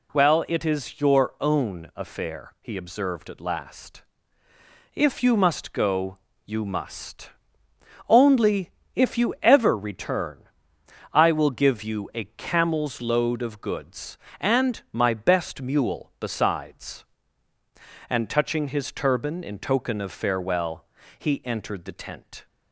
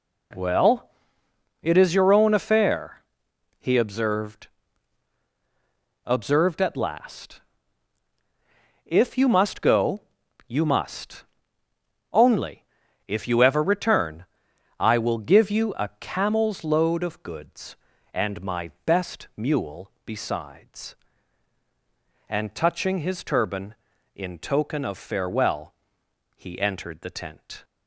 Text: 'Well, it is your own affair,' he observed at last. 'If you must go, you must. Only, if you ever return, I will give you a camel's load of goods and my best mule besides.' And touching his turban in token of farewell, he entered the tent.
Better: first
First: none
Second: says "observed" twice; at 6.0 s

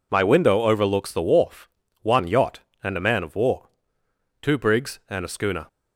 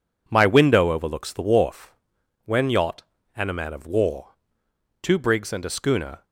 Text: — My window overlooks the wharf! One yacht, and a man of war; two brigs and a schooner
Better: first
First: none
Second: says "When" for "One"; at 2.4 s

